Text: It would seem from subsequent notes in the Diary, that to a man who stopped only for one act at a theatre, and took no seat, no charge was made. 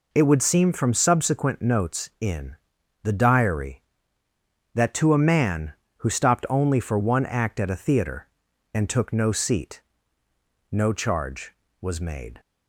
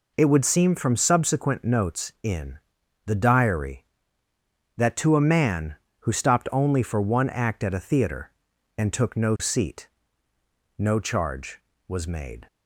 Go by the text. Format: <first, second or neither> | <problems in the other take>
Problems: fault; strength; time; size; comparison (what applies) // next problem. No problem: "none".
neither | pauses between "in" and "the"; noticeable; the same in both